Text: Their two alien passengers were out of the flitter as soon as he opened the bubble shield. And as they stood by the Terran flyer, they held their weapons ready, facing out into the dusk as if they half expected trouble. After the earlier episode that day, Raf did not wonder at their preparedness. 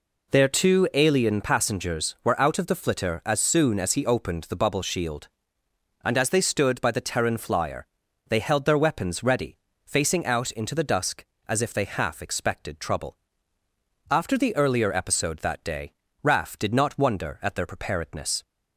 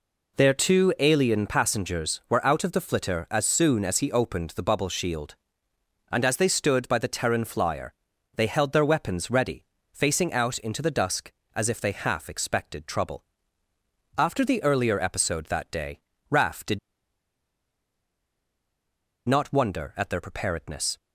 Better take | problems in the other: first | pauses between "did" and "not"; strong; at 16.7 s; 2.4 s long

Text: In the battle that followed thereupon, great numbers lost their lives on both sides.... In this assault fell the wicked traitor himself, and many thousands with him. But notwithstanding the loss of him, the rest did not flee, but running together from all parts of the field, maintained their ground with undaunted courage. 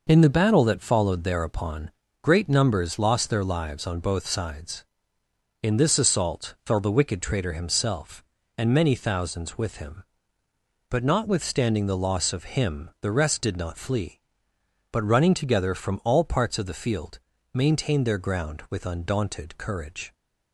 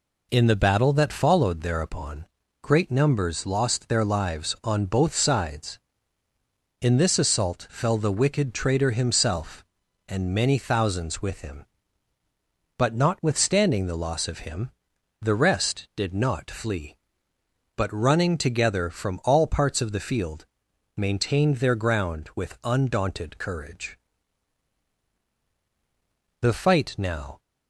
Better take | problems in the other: first | goes on to say "The fight now"; noticeable; from 26.3 s on; 1.0 s long

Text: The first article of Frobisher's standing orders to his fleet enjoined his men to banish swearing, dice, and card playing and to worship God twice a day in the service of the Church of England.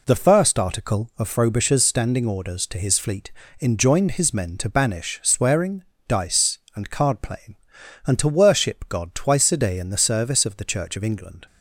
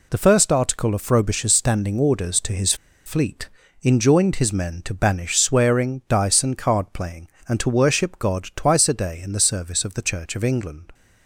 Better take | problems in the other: first | pauses between "his" and "fleet"; slight; at 2.7 s; 0.31 s long // pauses between "fleet" and "enjoined"; slight; at 3.4 s; 0.34 s long; slight in the first

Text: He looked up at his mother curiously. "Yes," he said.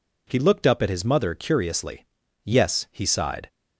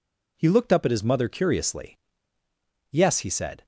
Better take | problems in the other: second | says "sighed" for "said"; at 3.0 s

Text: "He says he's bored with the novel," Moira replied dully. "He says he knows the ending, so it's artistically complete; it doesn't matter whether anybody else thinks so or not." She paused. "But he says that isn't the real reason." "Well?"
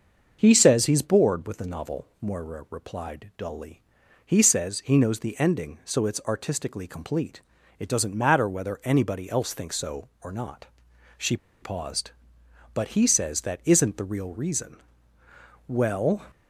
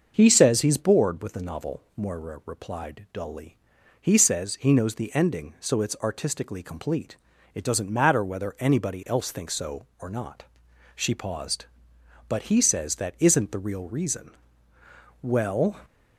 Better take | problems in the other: second | starts louder than the rest; until 1.4 s; 6.5 dB; also in the second // pauses between "She" and "paused"; slight; at 11.3 s; 0.26 s long

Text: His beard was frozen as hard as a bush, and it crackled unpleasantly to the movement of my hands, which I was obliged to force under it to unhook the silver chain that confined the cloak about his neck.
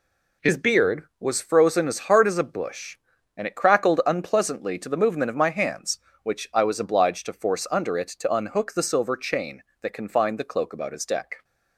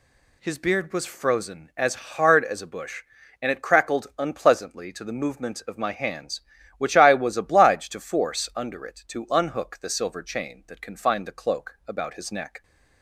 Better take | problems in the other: second | says "deck" for "neck"; at 11.0 s

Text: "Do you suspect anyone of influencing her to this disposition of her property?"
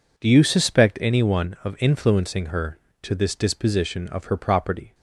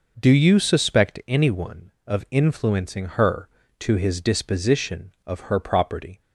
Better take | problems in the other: first | says "his" for "this"; at 3.9 s

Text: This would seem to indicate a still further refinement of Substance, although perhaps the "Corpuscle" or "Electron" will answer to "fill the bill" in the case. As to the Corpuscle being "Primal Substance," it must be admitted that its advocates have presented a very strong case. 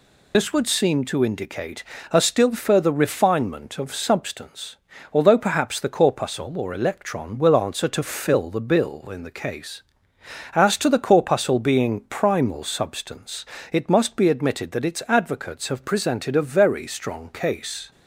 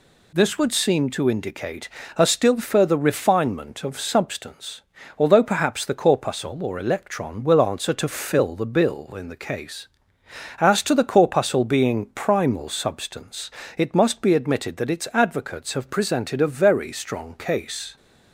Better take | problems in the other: second | loses the start of "This"; at 0.3 s; 65 ms // pauses between "indicate" and "a"; slight; at 1.8 s; 0.28 s long; slight in the second

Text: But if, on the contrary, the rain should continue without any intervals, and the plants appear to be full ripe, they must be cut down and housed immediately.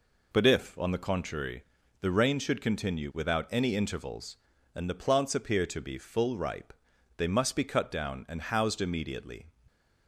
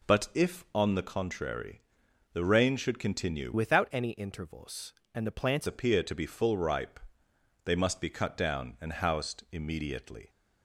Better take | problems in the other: first | changes voice from "without" to "plants"; from 3.5 to 5.6 s; 2.1 s long

